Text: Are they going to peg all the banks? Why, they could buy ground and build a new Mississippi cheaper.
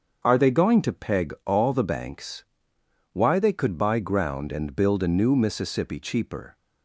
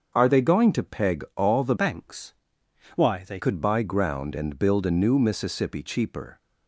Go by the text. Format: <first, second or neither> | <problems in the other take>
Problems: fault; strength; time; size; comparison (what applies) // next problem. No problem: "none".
first | starts louder than the rest; until 1.1 s; 6.5 dB; also in the first // changes voice from "banks" to "they"; from 1.7 to 3.3 s; 1.6 s long